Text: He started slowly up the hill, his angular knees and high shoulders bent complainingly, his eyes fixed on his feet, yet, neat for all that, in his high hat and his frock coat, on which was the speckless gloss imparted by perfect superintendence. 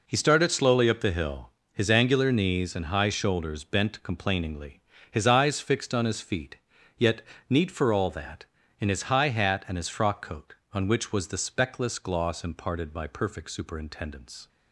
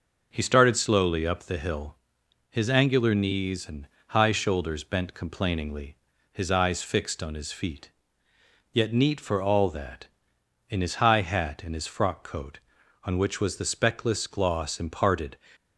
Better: first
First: none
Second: pauses between "and" and "high"; slight; at 3.8 s; 0.22 s long // stops before "by perfect superintendence"; at 15.5 s

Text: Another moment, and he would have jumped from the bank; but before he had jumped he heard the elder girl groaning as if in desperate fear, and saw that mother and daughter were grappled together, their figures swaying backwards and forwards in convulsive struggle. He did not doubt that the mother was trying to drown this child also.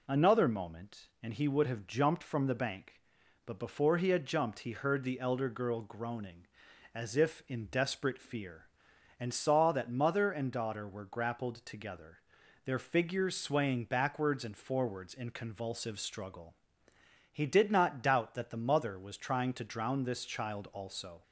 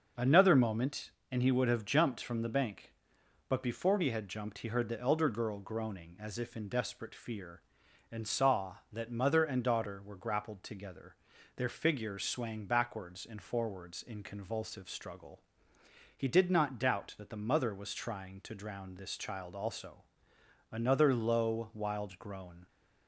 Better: first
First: none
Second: starts louder than the rest; until 1.3 s; 6 dB // goes on to say "Another low wild groan"; strong; from 20.7 s on; 1.9 s long

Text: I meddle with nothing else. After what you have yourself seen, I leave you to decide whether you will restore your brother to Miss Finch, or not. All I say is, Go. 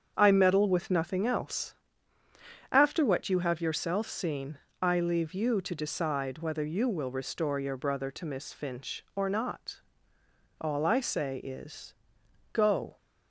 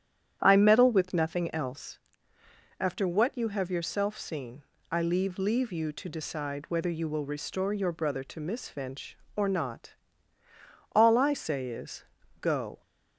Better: first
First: starts louder than the rest; strong; until 1.1 s; 7.5 dB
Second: starts louder than the rest; strong; until 1.4 s; 10 dB // says "leave" twice; at 5.3 s

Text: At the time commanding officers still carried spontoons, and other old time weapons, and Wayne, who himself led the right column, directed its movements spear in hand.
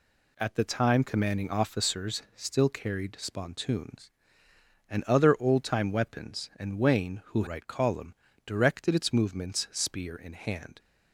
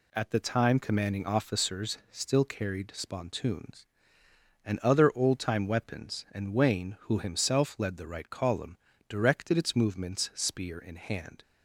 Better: second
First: skips "himself led the"; at 7.4 s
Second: none

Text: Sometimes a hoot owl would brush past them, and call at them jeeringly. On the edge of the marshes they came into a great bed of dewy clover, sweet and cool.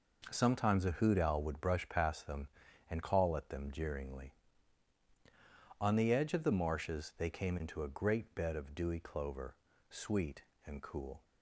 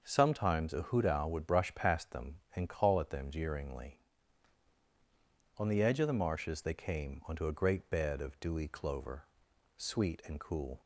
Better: first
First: none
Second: starts louder than the rest; until 1.0 s; 6 dB // says "onto" for "into"; at 7.2 s

